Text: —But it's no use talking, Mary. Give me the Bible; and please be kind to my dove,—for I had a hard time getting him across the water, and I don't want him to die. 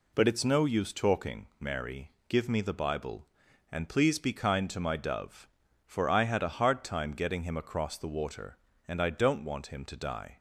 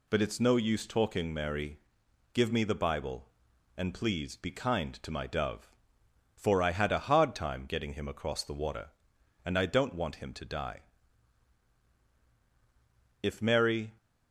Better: first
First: none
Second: goes on to say "If Mary"; noticeable; from 13.2 s on; 0.74 s long

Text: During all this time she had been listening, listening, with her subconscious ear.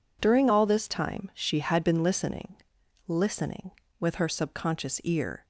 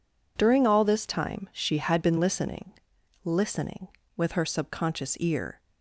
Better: neither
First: none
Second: none

